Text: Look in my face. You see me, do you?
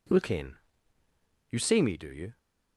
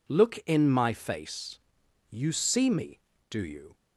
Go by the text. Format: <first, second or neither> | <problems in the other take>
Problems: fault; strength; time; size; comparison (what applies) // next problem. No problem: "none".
second | skips "my face"; at 1.0 s